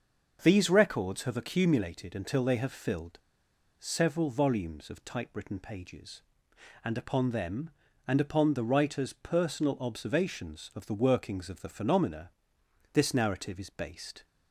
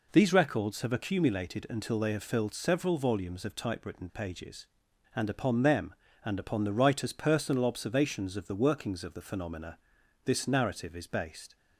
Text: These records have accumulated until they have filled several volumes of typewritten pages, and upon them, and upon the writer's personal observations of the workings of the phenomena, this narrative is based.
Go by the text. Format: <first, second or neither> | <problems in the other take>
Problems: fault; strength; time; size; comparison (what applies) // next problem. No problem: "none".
second | starts louder than the rest; until 1.4 s; 6.5 dB // pauses between "filled" and "several"; noticeable; at 3.1 s; 0.60 s long